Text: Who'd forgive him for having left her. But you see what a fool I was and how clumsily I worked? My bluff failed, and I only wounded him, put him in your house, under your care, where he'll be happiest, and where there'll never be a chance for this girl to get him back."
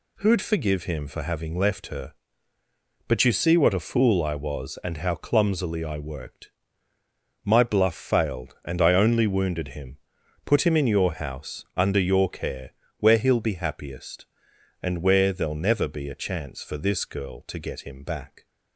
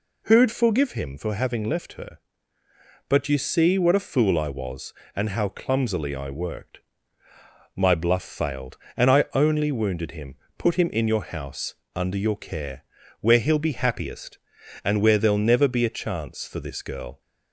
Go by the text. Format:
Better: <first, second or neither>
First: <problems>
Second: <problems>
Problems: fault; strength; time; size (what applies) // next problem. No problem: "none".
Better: first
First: none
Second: stops before "to get him back"; at 17.2 s